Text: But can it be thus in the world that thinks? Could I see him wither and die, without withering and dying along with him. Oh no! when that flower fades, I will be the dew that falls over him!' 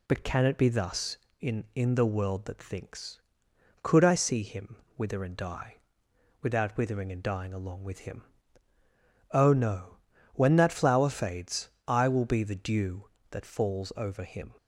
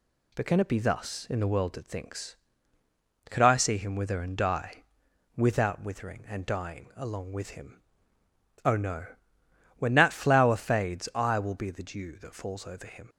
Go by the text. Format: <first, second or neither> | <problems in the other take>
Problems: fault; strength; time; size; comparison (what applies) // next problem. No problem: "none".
second | says "in" twice; at 1.7 s // pauses between "him" and "wither"; slight; at 4.7 s; 0.22 s long